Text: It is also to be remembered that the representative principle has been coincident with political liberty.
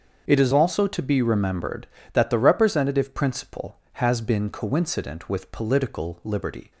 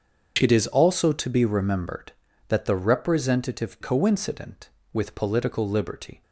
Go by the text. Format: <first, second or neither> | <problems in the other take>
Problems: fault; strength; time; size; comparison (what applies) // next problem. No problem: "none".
first | starts louder than the rest; until 1.4 s; 7 dB; also in the first // skips "principle has been"; at 3.7 s